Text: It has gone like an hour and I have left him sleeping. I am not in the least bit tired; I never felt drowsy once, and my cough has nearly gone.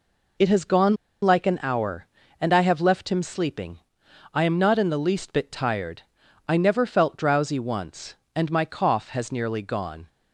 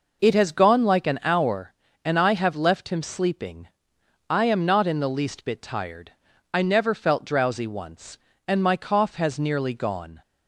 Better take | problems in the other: second | pauses between "gone" and "like"; slight; at 0.9 s; 0.26 s long

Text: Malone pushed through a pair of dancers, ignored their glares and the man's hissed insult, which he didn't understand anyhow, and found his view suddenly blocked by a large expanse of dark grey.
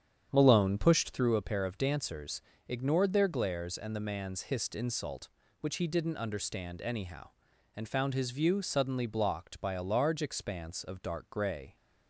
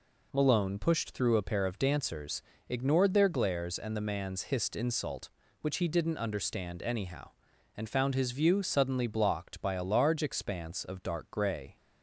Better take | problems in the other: second | starts louder than the rest; strong; until 1.3 s; 8.5 dB

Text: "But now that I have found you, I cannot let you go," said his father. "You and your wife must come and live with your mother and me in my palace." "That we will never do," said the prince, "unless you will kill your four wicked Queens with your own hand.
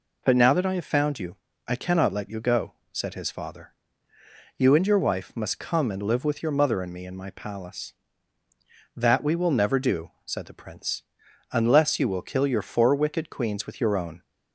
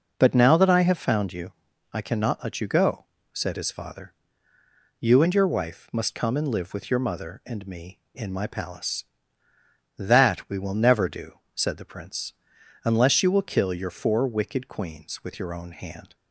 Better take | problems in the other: second | stops before "hand"; at 14.2 s

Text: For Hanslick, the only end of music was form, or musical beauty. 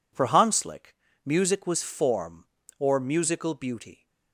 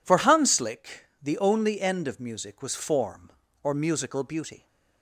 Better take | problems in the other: second | skips "the only end of"; at 1.0 s

